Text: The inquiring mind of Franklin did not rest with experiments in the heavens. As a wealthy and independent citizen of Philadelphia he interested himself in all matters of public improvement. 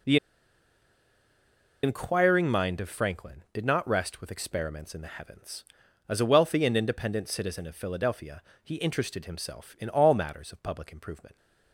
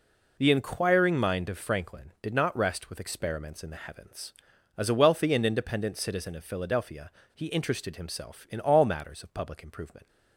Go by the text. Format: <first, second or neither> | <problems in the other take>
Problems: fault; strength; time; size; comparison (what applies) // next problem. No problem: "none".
second | pauses between "The" and "inquiring"; strong; at 0.1 s; 1.6 s long // pauses between "Philadelphia" and "he"; slight; at 8.4 s; 0.20 s long; slight in the second